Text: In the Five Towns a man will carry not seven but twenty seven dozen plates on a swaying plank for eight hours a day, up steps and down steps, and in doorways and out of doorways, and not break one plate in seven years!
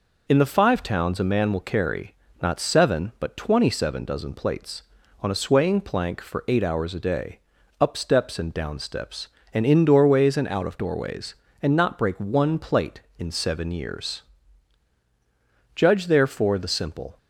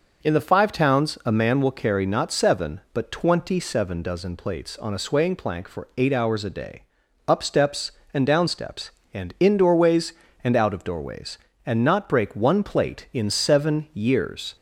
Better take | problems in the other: second | pauses between "carry" and "not"; slight; at 2.1 s; 0.26 s long // goes on to say "Judge therefore the simple"; from 15.7 s on; 1.4 s long

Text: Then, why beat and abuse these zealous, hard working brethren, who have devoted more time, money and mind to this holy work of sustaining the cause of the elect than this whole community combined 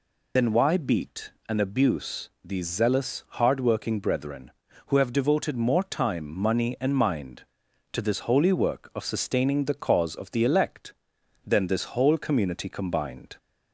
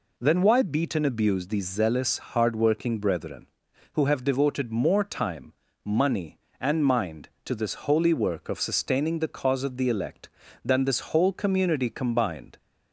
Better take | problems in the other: second | loses the start of "Then"; at 0.3 s; 80 ms

